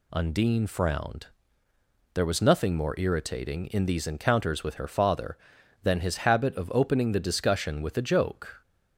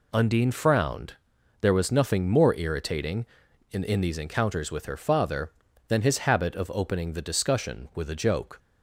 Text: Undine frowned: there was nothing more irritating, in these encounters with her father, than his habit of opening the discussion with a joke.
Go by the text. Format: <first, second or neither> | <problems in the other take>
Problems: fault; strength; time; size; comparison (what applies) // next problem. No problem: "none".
first | says "in" twice; at 3.8 s